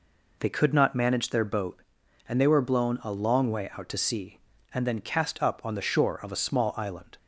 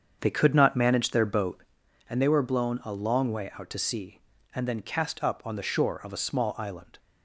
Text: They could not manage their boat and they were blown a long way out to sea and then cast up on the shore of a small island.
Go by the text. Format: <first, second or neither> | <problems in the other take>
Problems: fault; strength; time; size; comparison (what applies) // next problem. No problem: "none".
first | starts louder than the rest; strong; until 2.0 s; 7 dB